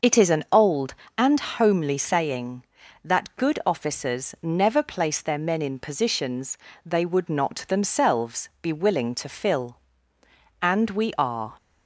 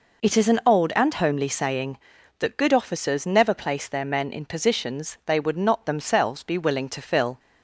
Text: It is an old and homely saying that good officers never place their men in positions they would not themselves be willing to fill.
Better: second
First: starts louder than the rest; noticeable; until 1.3 s; 6 dB // pauses between "positions" and "they"; slight; at 6.5 s; 0.28 s long // goes on to say "And we are"; noticeable; from 10.6 s on; 0.96 s long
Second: none

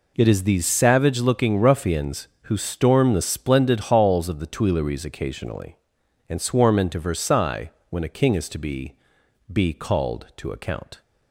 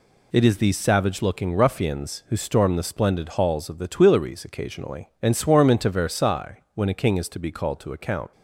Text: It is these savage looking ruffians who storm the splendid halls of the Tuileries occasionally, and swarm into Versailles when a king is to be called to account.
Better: second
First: pauses between "Versailles" and "when"; slight; at 7.7 s; 0.18 s long // says "be" twice; at 9.5 s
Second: none

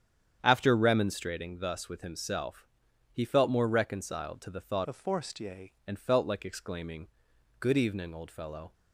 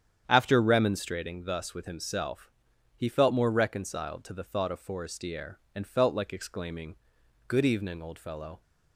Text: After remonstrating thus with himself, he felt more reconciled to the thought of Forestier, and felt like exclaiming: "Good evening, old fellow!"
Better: second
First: starts louder than the rest; strong; until 1.4 s; 8.5 dB // changes voice from "of" to "Forestier"; from 4.8 to 5.7 s; 0.9 s long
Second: starts louder than the rest; strong; until 1.2 s; 8.5 dB

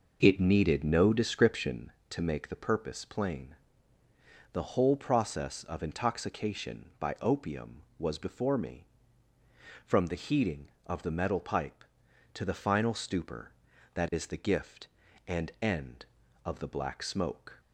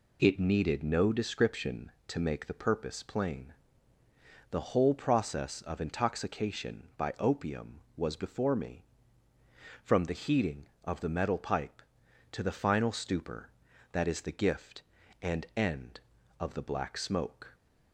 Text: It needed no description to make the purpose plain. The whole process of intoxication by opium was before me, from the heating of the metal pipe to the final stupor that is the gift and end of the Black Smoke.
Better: second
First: starts louder than the rest; noticeable; until 1.8 s; 5.5 dB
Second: none

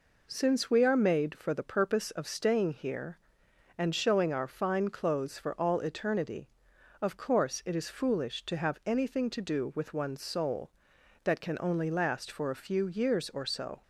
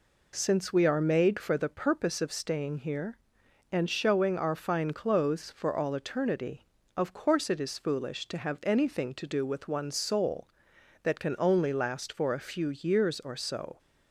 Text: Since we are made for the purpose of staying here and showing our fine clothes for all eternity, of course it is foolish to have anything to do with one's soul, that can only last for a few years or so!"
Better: neither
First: none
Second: none

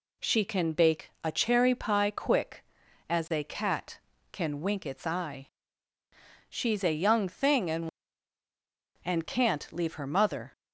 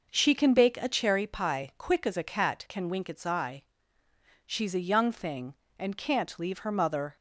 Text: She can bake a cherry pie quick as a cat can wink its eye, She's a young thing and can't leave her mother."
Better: second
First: says "and" twice; at 9.0 s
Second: none

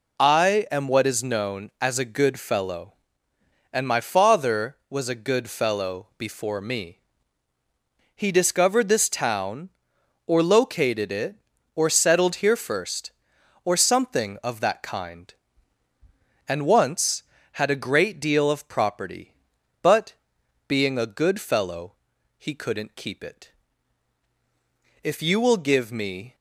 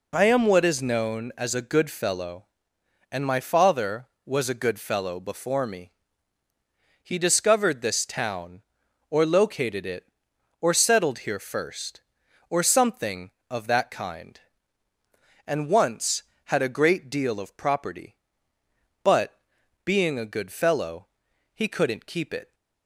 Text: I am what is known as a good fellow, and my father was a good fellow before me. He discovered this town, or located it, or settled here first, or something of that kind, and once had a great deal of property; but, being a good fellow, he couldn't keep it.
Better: second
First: goes on to say "If you will give me"; from 25.0 s on; 1.3 s long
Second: none

